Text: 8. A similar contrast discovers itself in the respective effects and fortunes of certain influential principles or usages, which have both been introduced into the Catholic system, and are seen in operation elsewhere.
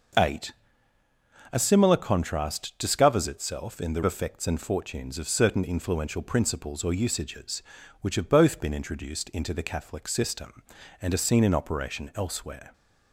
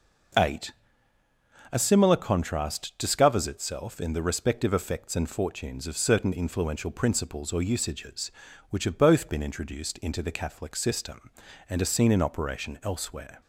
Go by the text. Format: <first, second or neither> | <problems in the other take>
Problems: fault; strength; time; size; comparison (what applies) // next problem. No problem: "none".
second | starts louder than the rest; noticeable; until 2.1 s; 6 dB // skips "respective"; at 4.0 s